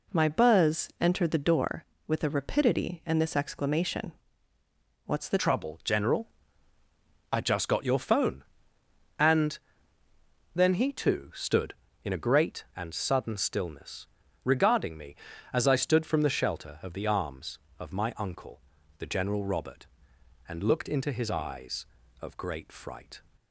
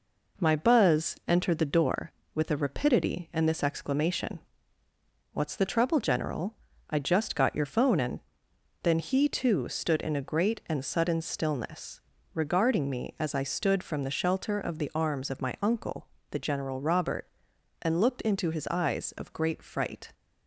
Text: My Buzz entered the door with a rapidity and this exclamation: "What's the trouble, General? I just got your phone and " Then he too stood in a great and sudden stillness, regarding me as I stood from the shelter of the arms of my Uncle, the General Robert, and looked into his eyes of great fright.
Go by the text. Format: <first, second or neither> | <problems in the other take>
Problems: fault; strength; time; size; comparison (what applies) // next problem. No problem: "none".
second | changes voice at "trouble"; from 5.3 s on; 17.9 s long